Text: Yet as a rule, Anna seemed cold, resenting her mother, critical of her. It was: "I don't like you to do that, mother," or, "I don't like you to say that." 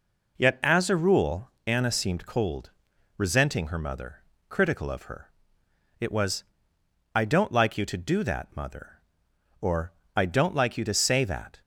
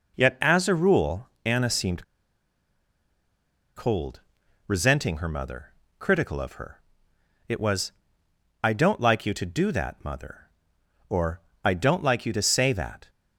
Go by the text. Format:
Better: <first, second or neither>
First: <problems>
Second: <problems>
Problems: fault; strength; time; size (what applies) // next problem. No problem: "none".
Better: first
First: none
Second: pauses between "seemed" and "cold"; strong; at 2.0 s; 1.7 s long